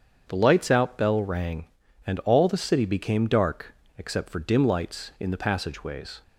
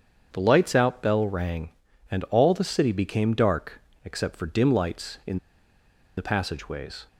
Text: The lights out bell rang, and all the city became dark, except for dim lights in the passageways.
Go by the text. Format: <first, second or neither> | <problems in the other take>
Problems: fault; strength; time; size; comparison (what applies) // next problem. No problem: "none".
first | starts louder than the rest; strong; until 1.3 s; 7.5 dB; strong in the first // pauses between "in" and "the"; noticeable; at 5.3 s; 0.78 s long